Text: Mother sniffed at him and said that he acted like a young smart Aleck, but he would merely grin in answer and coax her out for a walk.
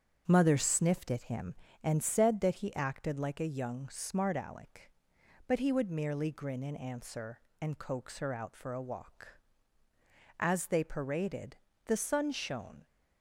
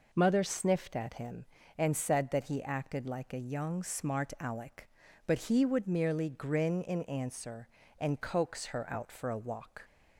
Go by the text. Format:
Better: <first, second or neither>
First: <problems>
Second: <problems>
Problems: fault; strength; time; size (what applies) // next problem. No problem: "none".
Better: second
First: starts louder than the rest; strong; until 1.2 s; 8 dB // goes on to say "As they paraded the sun shone"; strong; from 10.3 s on; 2.4 s long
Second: none